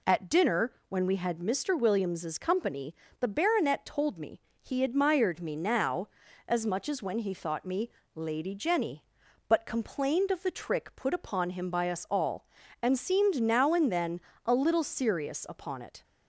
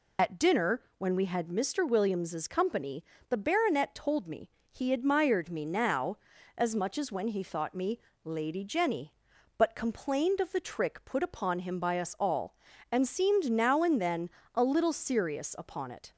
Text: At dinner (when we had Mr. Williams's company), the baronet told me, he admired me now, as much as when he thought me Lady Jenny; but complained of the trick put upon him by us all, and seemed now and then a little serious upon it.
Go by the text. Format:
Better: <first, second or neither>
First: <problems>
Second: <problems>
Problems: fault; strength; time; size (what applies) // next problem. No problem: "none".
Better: first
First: pauses between "me" and "Lady"; slight; at 7.8 s; 0.24 s long // pauses between "then" and "a"; slight; at 14.1 s; 0.26 s long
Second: loses the start of "At"; at 0.1 s; 50 ms // pauses between "me" and "Lady"; slight; at 7.9 s; 0.24 s long // pauses between "then" and "a"; slight; at 14.2 s; 0.26 s long